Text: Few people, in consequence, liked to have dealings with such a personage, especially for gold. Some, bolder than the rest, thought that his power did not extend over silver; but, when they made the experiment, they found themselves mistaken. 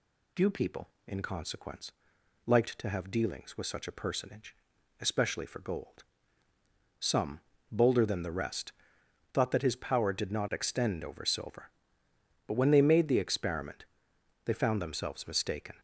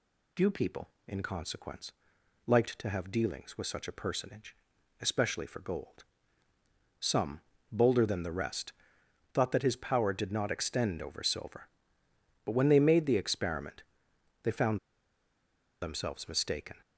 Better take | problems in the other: first | pauses between "found" and "themselves"; at 14.7 s; 1.0 s long

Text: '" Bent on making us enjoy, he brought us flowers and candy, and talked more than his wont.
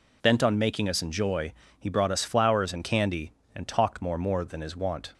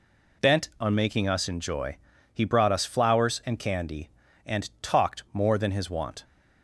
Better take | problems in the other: second | says "more" twice; at 4.1 s

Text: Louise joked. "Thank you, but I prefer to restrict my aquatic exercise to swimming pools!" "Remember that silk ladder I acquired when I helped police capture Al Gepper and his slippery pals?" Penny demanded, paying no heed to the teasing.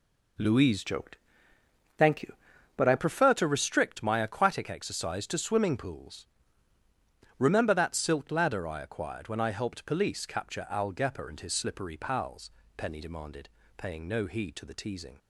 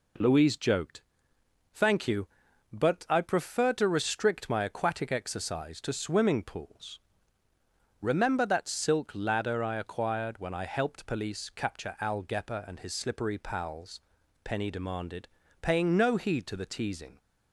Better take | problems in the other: second | changes voice from "joked" to "I"; from 0.8 to 2.9 s; 2.1 s long

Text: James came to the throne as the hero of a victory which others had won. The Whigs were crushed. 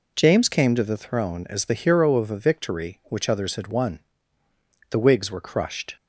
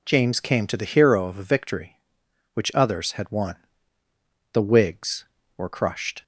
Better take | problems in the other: first | skips "throne as the"; at 0.8 s

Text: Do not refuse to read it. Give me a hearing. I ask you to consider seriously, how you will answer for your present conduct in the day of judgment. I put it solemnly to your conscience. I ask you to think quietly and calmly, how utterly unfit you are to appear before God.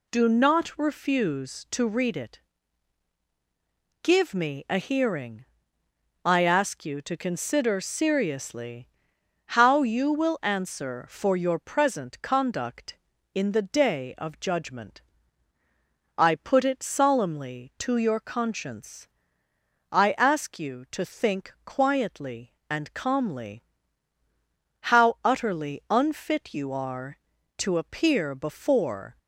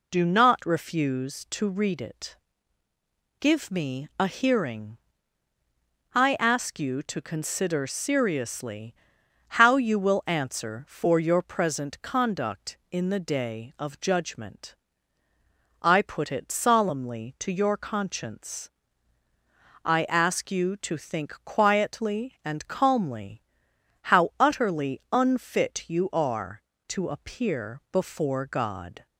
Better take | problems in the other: second | stops before "God"; at 29.1 s

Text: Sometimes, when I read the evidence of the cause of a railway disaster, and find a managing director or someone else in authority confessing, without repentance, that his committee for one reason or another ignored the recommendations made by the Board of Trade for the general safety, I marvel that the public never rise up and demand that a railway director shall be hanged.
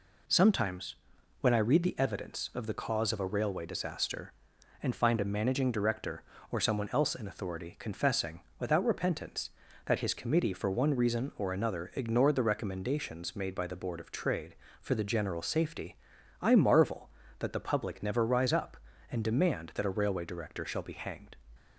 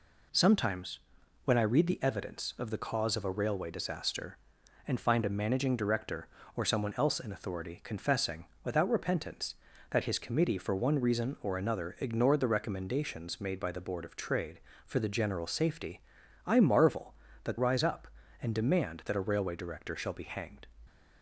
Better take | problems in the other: first | skips "the public never"; at 17.5 s

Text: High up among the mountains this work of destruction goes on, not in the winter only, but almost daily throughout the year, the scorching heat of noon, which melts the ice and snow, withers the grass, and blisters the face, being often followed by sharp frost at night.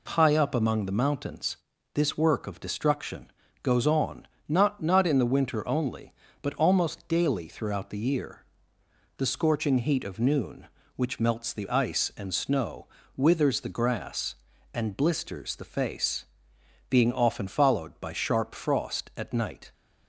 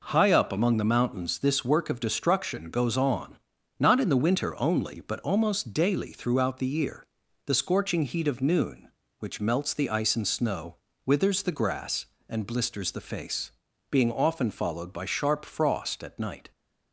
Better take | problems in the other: second | pauses between "mountains" and "this"; at 1.5 s; 0.38 s long // pauses between "destruction" and "goes"; slight; at 3.3 s; 0.30 s long // says "not" twice; at 4.8 s

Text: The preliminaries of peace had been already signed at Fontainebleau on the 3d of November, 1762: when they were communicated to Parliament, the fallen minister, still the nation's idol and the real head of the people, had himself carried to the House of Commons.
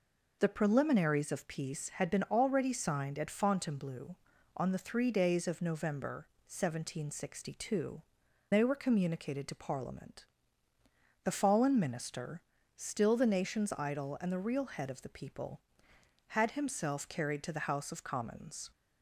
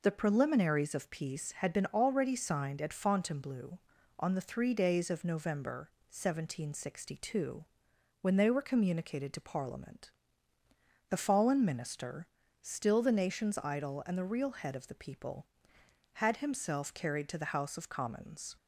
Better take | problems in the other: second | skips "when"; at 8.2 s

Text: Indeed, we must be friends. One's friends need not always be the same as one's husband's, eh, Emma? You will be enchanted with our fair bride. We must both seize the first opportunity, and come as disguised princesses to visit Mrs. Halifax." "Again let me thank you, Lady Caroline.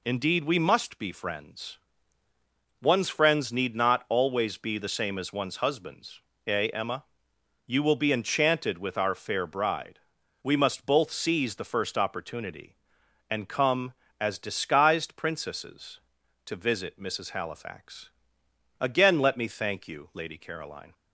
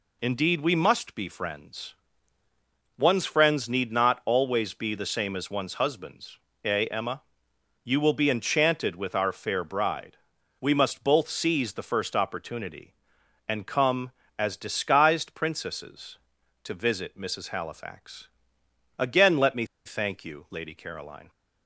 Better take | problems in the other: first | pauses between "me" and "thank"; slight; at 19.6 s; 0.18 s long

